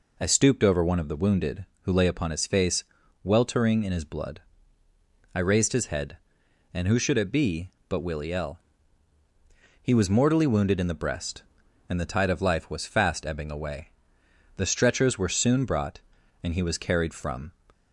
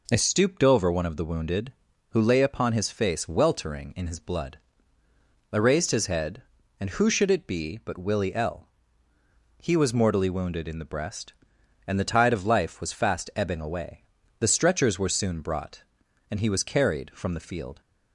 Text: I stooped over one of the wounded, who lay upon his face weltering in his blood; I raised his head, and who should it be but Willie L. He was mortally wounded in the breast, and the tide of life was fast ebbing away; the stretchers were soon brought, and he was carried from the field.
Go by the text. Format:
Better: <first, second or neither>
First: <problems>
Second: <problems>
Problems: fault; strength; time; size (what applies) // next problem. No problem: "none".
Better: second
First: pauses between "face" and "weltering"; at 2.8 s; 0.40 s long // stops before "the field"; at 17.7 s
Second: none